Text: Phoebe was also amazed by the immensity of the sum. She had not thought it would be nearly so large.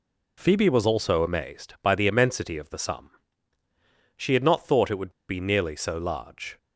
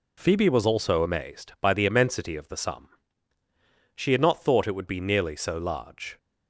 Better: second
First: pauses between "would" and "be"; slight; at 5.1 s; 0.18 s long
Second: none

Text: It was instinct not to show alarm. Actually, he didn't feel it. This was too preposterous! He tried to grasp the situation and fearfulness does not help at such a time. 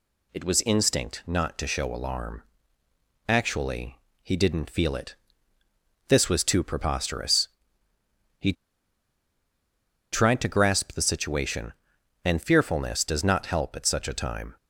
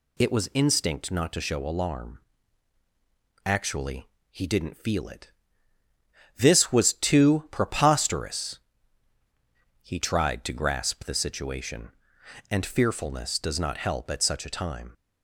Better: second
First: pauses between "He" and "tried"; strong; at 8.5 s; 1.5 s long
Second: none

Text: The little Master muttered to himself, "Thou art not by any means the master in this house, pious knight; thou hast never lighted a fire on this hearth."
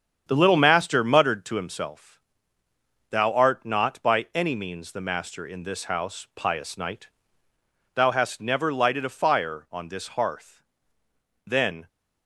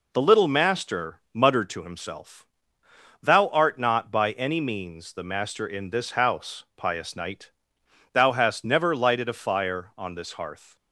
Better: second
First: starts louder than the rest; strong; until 1.2 s; 8 dB // goes on to say "Then"; slight; from 11.4 s on; 0.42 s long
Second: none

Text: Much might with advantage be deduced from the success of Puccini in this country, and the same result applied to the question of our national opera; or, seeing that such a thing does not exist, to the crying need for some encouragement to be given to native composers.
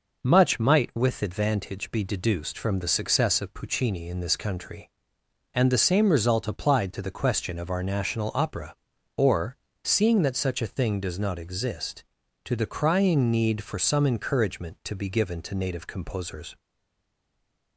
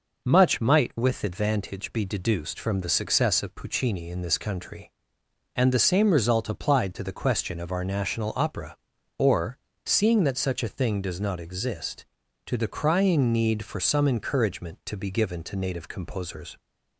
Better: second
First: stays silent after the last word; noticeable; from 16.5 s on; 1.2 s long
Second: none

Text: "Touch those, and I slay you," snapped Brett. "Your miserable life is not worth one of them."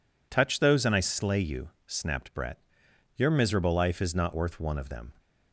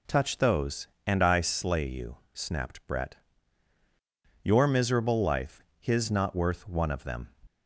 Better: first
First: none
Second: says "his" for "is"; at 5.7 s

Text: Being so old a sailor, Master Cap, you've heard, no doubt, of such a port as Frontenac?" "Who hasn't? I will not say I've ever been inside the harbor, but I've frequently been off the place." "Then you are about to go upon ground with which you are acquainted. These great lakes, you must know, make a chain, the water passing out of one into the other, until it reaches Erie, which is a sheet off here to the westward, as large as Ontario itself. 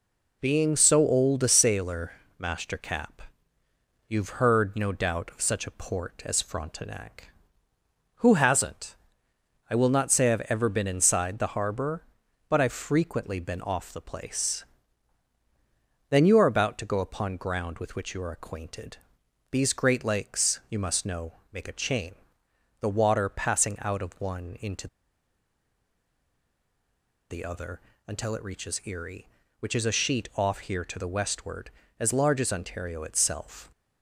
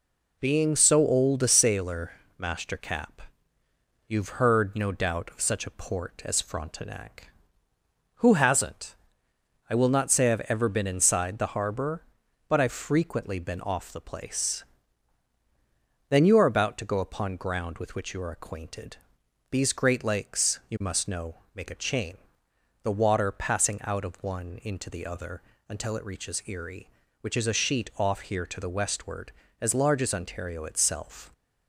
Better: second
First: pauses between "into" and "the"; strong; at 24.8 s; 2.4 s long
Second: none

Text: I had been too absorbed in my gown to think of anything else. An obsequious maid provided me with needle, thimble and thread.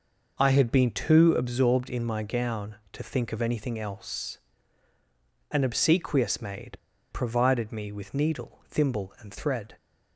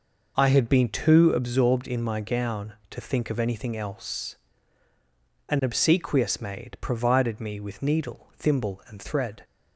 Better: second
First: pauses between "maid" and "provided"; slight; at 6.7 s; 0.35 s long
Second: none

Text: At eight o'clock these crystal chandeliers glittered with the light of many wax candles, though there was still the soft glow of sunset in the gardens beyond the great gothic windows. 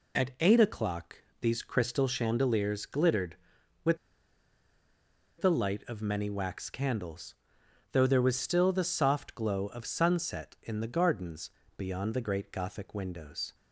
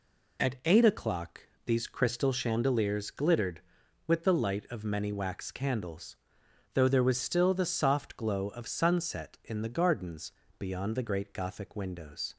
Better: second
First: pauses between "o'clock" and "these"; slight; at 1.1 s; 0.26 s long // pauses between "with" and "the"; strong; at 3.9 s; 1.4 s long // pauses between "gardens" and "beyond"; slight; at 11.4 s; 0.30 s long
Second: pauses between "o'clock" and "these"; slight; at 1.4 s; 0.26 s long // pauses between "gardens" and "beyond"; slight; at 10.2 s; 0.30 s long

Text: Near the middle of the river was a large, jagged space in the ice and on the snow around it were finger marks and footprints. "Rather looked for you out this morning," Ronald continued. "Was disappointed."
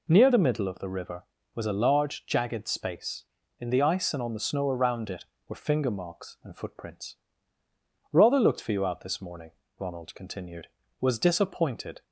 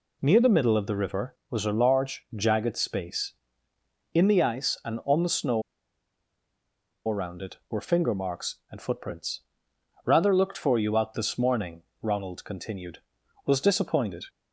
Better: first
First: none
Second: pauses between "snow" and "around"; strong; at 5.6 s; 1.4 s long

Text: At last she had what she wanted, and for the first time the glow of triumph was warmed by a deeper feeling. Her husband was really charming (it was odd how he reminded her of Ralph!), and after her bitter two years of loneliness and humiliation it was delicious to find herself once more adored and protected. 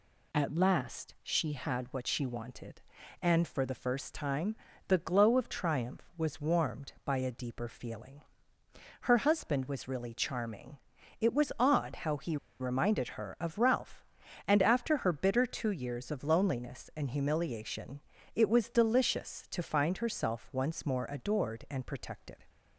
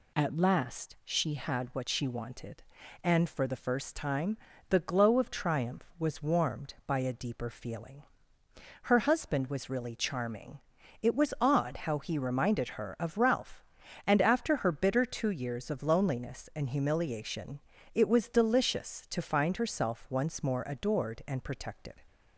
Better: second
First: pauses between "time" and "the"; slight; at 4.5 s; 0.32 s long // pauses between "he" and "reminded"; slight; at 12.3 s; 0.24 s long // pauses between "humiliation" and "it"; slight; at 18.0 s; 0.34 s long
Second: pauses between "time" and "the"; slight; at 4.3 s; 0.32 s long // pauses between "humiliation" and "it"; slight; at 17.6 s; 0.34 s long

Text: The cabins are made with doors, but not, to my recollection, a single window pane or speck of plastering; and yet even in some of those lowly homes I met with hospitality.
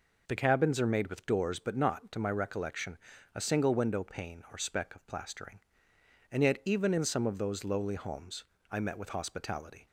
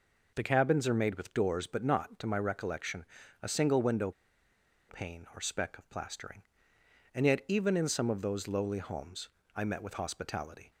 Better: first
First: pauses between "homes" and "I"; slight; at 8.4 s; 0.28 s long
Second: pauses between "window" and "pane"; noticeable; at 4.1 s; 0.77 s long // pauses between "homes" and "I"; slight; at 9.2 s; 0.28 s long

